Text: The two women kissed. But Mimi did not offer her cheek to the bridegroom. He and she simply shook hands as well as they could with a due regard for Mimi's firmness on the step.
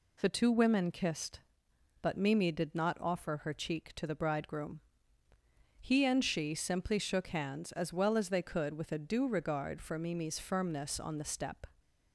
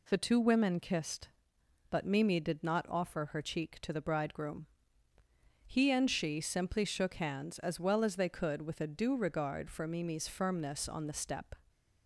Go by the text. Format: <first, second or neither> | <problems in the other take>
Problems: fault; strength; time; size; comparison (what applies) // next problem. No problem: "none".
neither | none